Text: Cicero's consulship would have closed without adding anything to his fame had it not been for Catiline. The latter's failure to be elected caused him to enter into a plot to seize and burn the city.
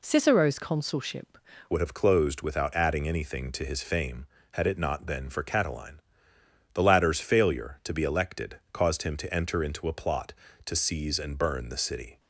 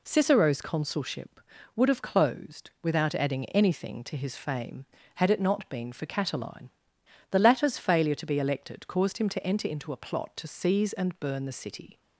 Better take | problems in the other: second | changes voice at "would"; from 1.7 s on; 10.4 s long

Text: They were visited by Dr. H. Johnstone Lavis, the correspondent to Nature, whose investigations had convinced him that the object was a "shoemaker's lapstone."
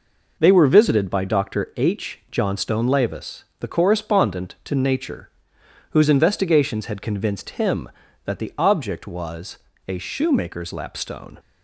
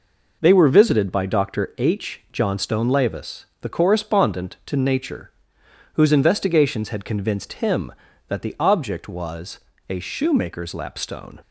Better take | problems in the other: neither | pauses between "was" and "a"; slight; the same in both

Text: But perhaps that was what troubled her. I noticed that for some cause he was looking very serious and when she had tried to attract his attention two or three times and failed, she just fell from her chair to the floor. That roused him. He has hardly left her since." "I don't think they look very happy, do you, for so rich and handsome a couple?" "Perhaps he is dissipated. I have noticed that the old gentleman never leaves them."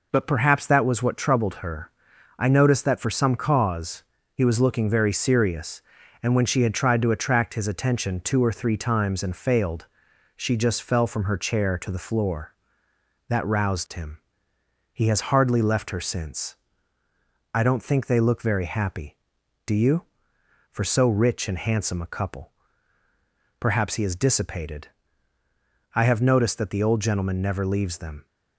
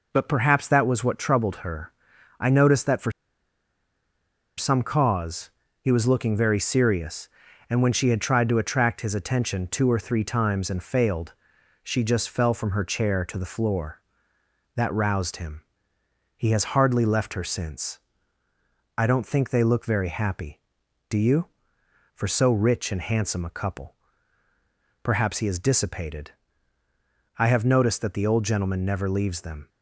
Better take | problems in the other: first | pauses between "for" and "some"; strong; at 3.1 s; 1.4 s long // pauses between "cause" and "he"; slight; at 5.5 s; 0.30 s long; slight in the first

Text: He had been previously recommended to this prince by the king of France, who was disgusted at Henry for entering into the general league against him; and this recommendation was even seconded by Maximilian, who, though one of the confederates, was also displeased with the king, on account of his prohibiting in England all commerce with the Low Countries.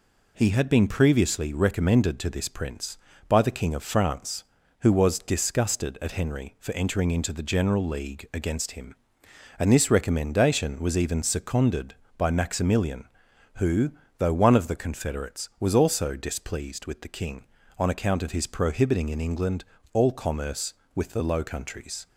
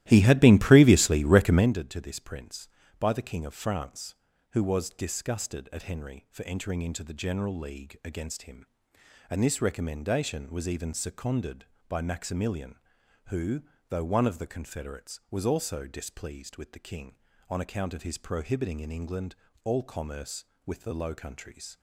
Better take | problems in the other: first | starts louder than the rest; strong; until 1.7 s; 15 dB // pauses between "England" and "all"; slight; at 19.3 s; 0.30 s long; slight in the first

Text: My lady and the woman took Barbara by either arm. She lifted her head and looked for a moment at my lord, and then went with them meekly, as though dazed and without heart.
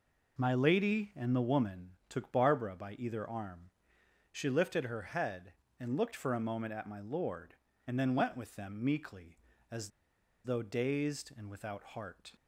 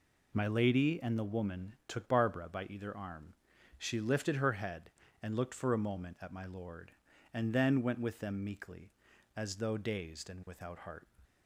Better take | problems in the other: second | pauses between "woman" and "took"; slight; at 1.9 s; 0.16 s long // pauses between "as" and "though"; noticeable; at 9.8 s; 0.55 s long

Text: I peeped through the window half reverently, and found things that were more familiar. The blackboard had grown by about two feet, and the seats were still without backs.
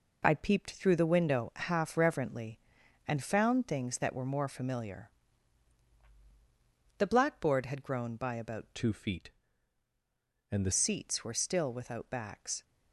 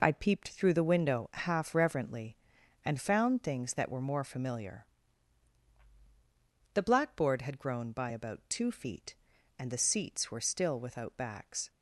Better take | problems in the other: second | changes voice from "two" to "the"; from 8.7 to 10.6 s; 1.9 s long

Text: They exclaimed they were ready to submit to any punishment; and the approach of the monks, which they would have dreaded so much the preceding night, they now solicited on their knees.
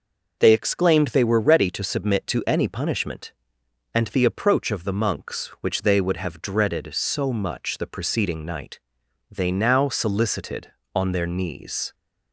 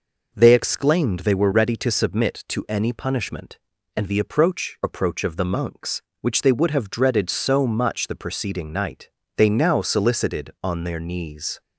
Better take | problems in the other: first | says "approach" twice; at 4.8 s

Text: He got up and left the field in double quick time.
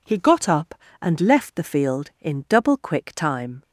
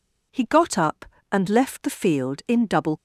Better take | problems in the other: first | stops before "quick time"; at 2.9 s

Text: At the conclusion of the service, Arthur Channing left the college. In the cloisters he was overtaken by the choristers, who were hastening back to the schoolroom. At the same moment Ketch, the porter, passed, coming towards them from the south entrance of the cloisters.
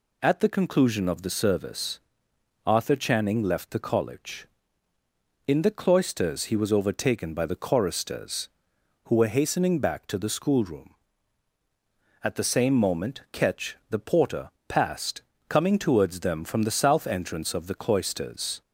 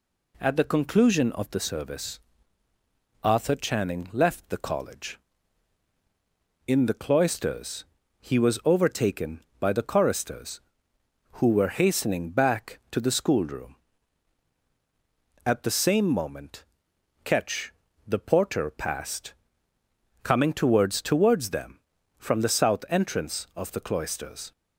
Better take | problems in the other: first | pauses between "cloisters" and "he"; slight; at 7.8 s; 0.34 s long // pauses between "moment" and "Ketch"; noticeable; at 16.6 s; 0.58 s long // says "towards" twice; at 20.9 s

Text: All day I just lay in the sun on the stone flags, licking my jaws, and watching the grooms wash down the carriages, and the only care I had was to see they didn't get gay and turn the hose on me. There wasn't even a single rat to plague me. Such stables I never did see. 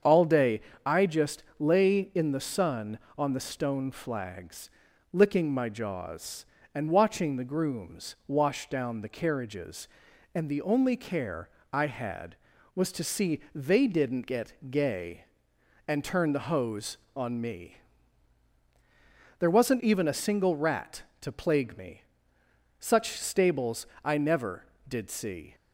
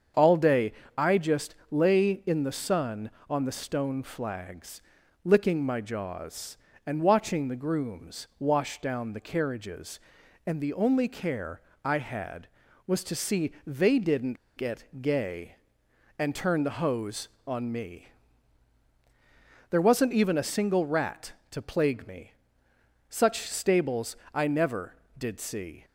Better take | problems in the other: first | starts louder than the rest; strong; until 1.4 s; 7 dB; strong in the first // pauses between "day" and "I"; slight; at 0.7 s; 0.26 s long; slight in the first // pauses between "care" and "I"; slight; at 11.5 s; 0.24 s long; slight in the first // pauses between "didn't" and "get"; slight; at 14.3 s; 0.19 s long // pauses between "get" and "gay"; slight; at 14.8 s; 0.16 s long; slight in the first // pauses between "stables" and "I"; slight; at 24.1 s; 0.16 s long; slight in the first

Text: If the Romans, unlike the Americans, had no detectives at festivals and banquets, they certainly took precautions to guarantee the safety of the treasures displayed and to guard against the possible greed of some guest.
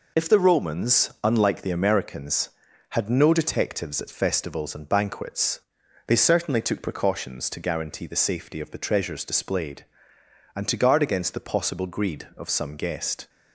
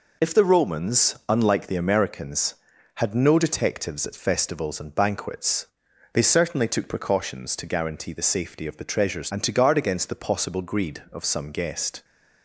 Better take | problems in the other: first | skips "displayed"; at 9.2 s

